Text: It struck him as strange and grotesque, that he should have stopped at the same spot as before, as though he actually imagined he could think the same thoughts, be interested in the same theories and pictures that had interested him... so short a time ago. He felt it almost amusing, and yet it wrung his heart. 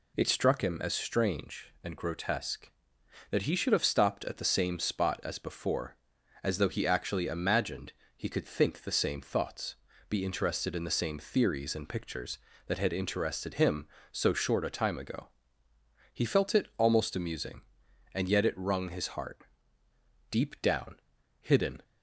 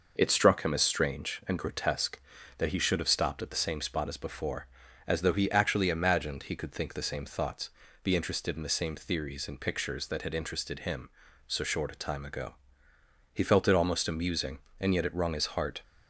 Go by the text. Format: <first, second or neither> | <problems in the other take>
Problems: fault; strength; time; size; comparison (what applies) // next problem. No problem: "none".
second | pauses between "imagined" and "he"; slight; at 7.9 s; 0.24 s long // goes on to say "Deep down hidden"; from 20.3 s on; 1.5 s long